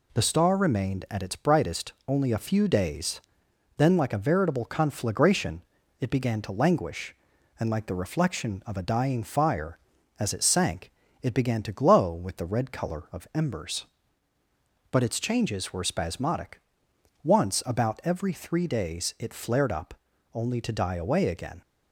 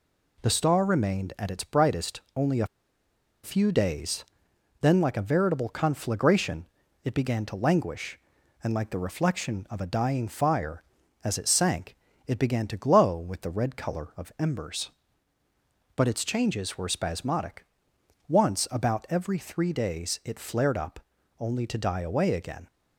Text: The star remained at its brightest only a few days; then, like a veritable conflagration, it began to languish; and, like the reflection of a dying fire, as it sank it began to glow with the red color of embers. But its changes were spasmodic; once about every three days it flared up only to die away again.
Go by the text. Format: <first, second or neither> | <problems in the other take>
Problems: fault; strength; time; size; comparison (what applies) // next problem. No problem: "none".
first | pauses between "a" and "few"; noticeable; at 2.6 s; 0.76 s long // pauses between "sank" and "it"; slight; at 11.9 s; 0.32 s long; slight in the first // pauses between "up" and "only"; at 20.9 s; 0.40 s long; also in the first